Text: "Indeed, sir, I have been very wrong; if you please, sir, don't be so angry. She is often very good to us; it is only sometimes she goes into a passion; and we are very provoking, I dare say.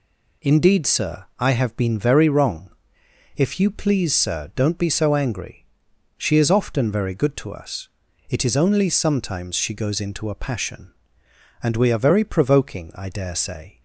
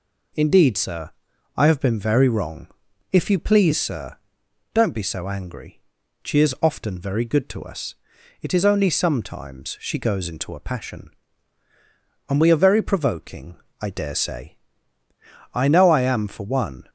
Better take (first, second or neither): first